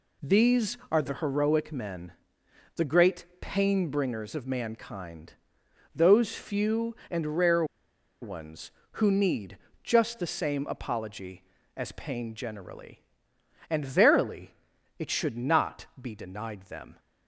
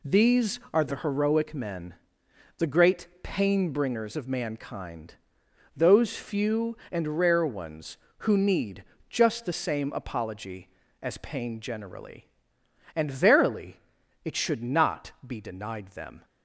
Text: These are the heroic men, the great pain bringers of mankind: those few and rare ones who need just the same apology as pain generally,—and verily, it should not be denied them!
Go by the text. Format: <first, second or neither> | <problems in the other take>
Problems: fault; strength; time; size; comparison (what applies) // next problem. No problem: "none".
second | pauses between "great" and "pain"; slight; at 3.2 s; 0.16 s long; slight in the second // pauses between "rare" and "ones"; noticeable; at 7.6 s; 0.58 s long // pauses between "need" and "just"; slight; at 9.5 s; 0.28 s long; slight in the second